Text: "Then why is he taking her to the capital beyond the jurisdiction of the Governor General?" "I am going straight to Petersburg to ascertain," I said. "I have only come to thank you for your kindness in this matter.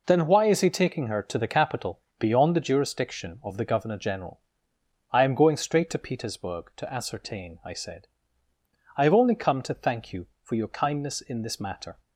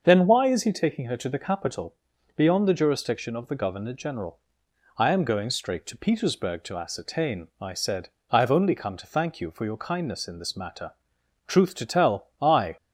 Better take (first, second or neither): first